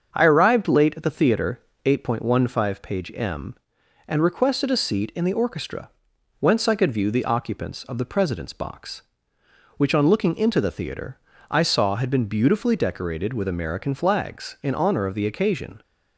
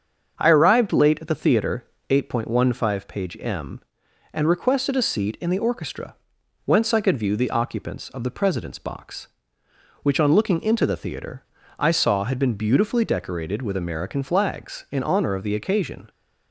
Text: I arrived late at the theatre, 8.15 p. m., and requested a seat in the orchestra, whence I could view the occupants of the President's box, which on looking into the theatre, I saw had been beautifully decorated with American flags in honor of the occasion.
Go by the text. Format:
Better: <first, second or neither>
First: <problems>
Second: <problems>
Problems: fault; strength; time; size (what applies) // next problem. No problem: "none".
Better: neither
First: starts louder than the rest; until 1.1 s; 7 dB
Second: starts louder than the rest; until 1.4 s; 7 dB